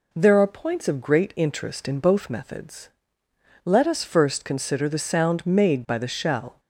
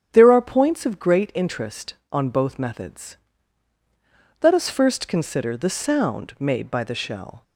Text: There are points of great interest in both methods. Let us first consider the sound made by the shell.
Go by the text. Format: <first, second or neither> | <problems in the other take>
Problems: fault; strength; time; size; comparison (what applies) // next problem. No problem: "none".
first | starts louder than the rest; strong; until 1.1 s; 9 dB // says "on" for "in"; at 2.1 s